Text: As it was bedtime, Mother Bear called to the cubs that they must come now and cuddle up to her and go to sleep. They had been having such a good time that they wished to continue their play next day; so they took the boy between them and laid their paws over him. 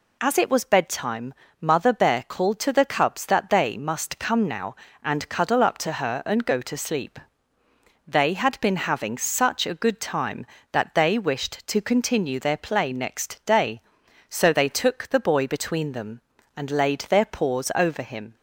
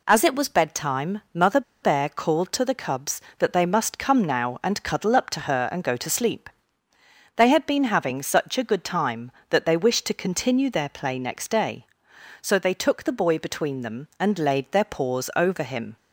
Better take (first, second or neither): first